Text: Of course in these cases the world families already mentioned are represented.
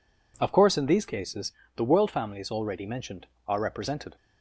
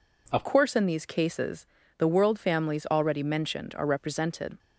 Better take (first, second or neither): first